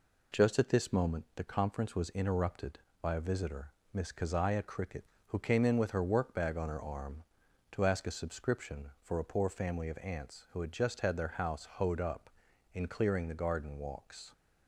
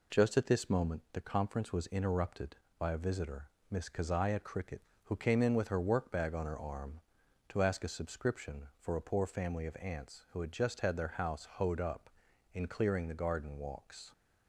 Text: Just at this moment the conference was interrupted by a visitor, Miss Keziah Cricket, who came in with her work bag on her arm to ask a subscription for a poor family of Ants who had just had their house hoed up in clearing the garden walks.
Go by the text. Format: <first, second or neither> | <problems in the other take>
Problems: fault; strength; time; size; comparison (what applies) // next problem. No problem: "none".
neither | none